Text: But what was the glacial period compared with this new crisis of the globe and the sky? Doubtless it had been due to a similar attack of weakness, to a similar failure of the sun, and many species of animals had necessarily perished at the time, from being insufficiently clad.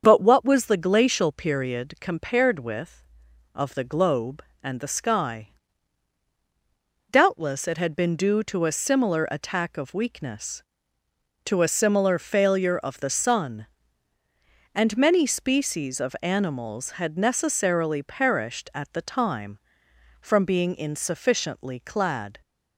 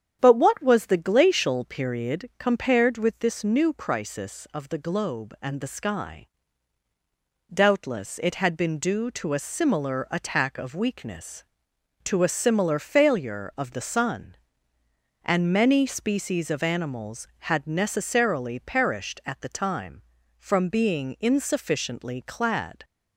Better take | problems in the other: second | starts louder than the rest; strong; until 1.0 s; 7 dB; strong in the second // skips "this new crisis"; at 3.2 s

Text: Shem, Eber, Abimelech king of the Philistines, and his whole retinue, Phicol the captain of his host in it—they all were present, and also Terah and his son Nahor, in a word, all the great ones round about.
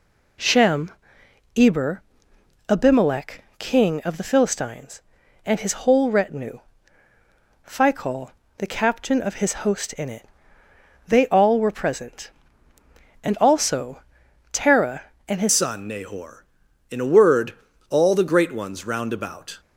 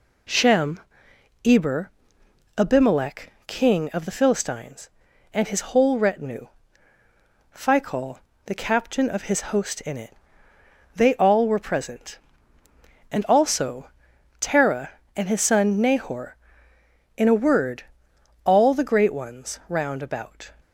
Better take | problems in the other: second | pauses between "Phicol" and "the"; slight; at 8.3 s; 0.26 s long; slight in the second // pauses between "also" and "Terah"; noticeable; at 14.0 s; 0.52 s long; noticeable in the second // changes voice at "son"; from 15.4 s on; 4.1 s long

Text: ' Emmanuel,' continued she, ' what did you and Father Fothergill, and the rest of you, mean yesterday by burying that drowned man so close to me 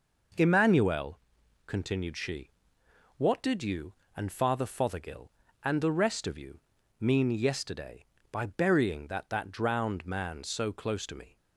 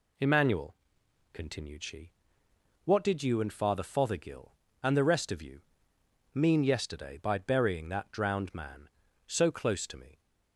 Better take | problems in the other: second | says "that" twice; at 9.2 s

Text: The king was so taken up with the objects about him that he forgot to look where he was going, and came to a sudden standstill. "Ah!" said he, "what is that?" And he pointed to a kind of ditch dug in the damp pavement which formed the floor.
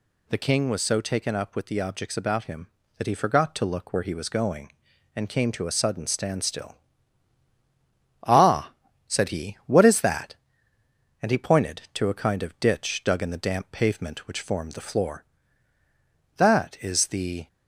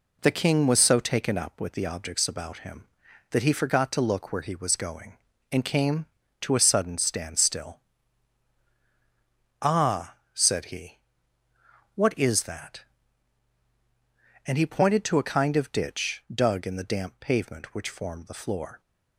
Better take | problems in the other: second | goes on to say "That is the"; noticeable; from 16.3 s on; 1.1 s long

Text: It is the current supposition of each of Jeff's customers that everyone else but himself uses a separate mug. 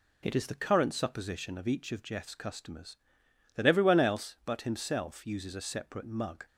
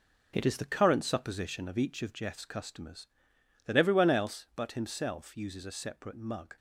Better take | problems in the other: first | gets quieter; strong; throughout; 7.5 dB

